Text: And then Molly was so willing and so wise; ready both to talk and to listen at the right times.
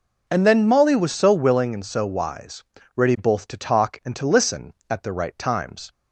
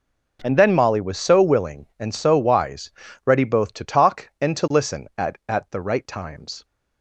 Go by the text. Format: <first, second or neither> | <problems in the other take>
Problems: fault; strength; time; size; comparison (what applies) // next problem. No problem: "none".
first | says "at" twice; at 5.4 s